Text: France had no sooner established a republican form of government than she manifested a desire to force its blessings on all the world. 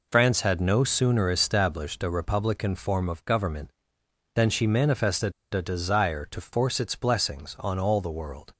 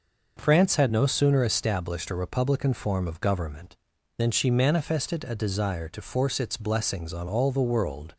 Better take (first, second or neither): second